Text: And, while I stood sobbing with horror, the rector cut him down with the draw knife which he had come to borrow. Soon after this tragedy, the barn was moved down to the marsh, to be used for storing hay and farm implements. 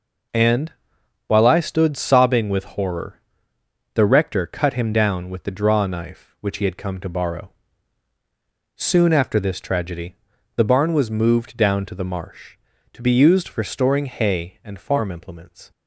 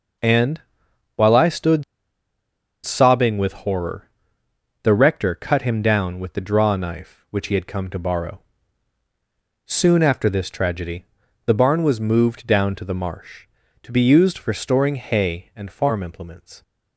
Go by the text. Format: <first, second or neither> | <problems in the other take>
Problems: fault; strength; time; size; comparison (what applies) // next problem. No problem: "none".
first | pauses between "stood" and "sobbing"; at 1.8 s; 1.0 s long